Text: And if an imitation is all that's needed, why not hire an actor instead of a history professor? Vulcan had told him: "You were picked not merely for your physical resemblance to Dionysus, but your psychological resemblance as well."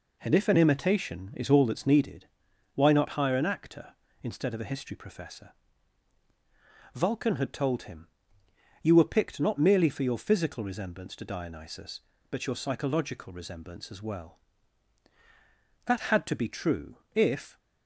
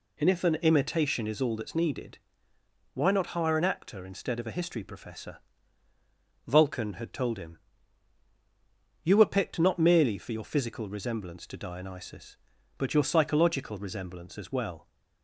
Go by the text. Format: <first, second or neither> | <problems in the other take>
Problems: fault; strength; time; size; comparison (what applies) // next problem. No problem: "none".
second | goes on to say "That had to be true if"; strong; from 15.8 s on; 1.7 s long